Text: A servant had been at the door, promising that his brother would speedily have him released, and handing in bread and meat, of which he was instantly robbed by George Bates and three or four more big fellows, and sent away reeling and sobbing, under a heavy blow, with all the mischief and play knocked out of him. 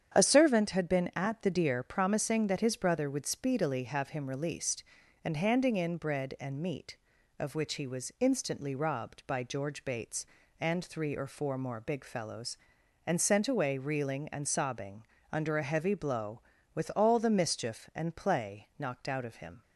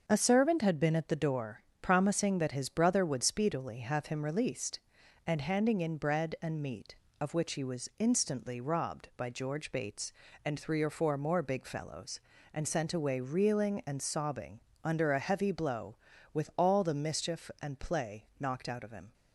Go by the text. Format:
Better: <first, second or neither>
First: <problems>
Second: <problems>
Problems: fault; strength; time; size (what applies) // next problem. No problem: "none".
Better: second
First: starts louder than the rest; strong; until 1.2 s; 8.5 dB // says "deer" for "door"; at 1.4 s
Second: starts louder than the rest; until 1.0 s; 6.5 dB